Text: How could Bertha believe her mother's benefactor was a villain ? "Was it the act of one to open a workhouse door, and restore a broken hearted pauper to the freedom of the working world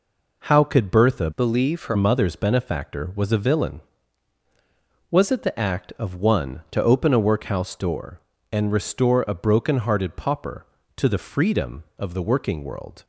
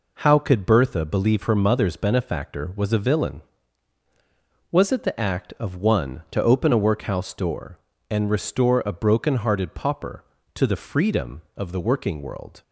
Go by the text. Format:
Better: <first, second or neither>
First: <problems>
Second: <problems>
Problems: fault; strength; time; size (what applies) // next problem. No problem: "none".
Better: second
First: changes voice from "believe" to "her"; from 1.3 to 1.9 s; 0.6 s long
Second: none